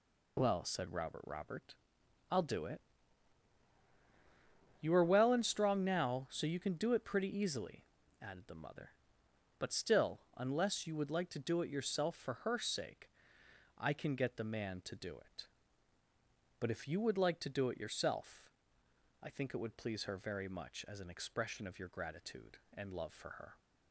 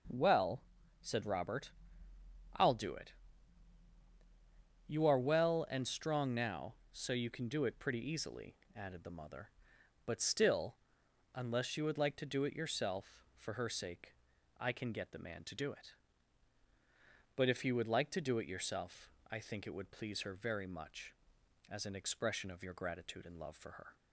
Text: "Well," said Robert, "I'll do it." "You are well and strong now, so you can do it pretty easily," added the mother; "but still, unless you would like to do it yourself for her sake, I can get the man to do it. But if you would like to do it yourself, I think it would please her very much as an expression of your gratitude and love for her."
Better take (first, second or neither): second